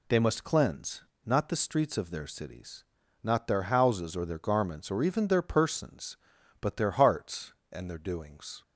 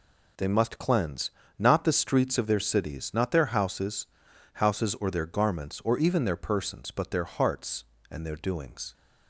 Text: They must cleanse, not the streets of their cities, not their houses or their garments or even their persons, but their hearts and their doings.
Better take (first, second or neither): first